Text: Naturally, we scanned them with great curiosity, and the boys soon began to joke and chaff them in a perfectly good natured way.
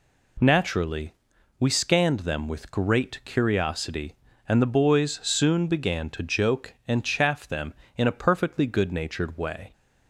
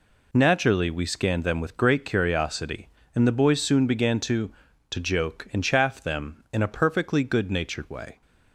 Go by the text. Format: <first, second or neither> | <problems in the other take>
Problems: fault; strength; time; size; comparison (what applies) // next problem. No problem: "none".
first | says "to" twice; at 4.8 s